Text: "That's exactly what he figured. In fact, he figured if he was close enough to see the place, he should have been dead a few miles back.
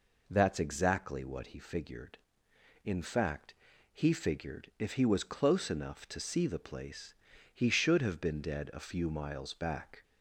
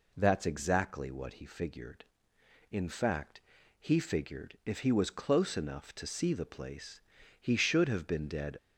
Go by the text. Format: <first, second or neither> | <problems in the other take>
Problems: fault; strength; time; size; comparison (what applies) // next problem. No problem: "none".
first | stops before "a few miles back"; at 8.5 s